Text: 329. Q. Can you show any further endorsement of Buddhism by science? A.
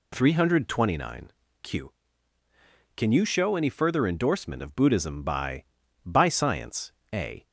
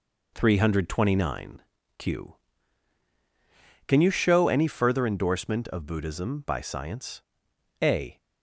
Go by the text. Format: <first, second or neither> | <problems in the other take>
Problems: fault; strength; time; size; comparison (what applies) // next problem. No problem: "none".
second | says "by" twice; at 6.0 s